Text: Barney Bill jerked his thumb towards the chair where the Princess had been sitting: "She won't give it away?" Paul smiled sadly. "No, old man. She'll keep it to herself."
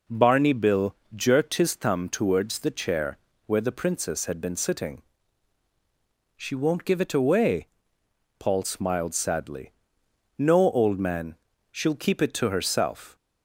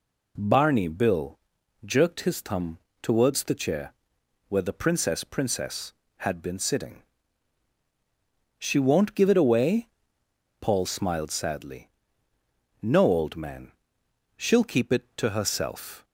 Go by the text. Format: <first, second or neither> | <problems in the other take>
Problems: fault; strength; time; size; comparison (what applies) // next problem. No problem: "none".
first | pauses between "Bill" and "jerked"; at 1.3 s; 0.44 s long; slight in the first // pauses between "thumb" and "towards"; slight; at 2.7 s; 0.24 s long // pauses between "chair" and "where"; noticeable; at 3.9 s; 0.56 s long; slight in the first // says "Princess" twice; at 5.2 s